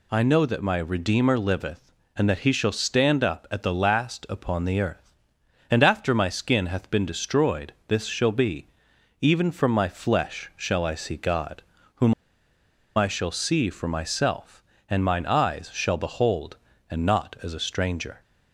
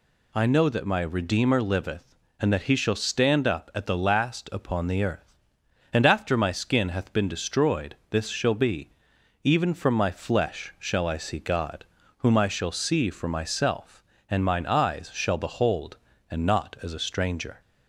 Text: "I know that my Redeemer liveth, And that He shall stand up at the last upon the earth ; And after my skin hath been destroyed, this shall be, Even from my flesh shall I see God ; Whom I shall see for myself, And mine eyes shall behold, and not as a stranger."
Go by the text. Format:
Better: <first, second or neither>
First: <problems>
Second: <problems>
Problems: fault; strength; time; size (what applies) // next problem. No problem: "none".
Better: second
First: pauses between "Whom" and "I"; noticeable; at 12.1 s; 0.83 s long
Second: none